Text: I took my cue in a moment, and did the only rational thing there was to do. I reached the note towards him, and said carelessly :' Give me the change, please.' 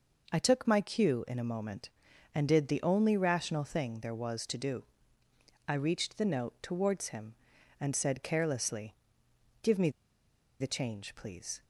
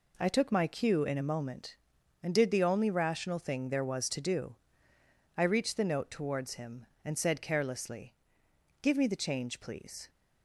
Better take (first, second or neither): second